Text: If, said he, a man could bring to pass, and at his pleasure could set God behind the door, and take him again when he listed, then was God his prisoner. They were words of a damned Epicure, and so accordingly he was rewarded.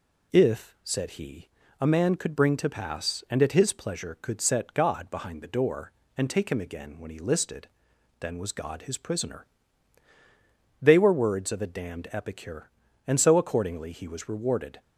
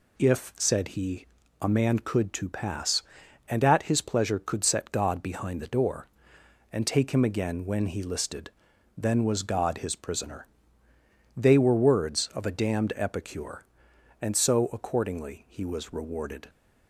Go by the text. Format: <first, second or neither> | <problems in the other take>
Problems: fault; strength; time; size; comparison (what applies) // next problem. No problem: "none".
first | skips "bring"; at 2.3 s